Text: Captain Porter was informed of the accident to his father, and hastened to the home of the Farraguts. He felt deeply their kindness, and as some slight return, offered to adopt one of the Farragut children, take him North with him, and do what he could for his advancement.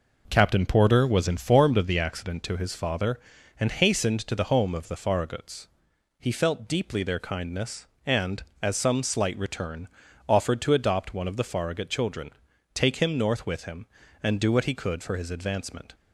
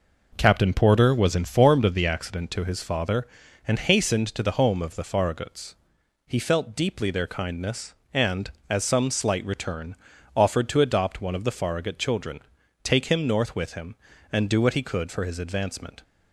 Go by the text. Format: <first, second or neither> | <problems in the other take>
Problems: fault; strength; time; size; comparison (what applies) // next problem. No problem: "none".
neither | none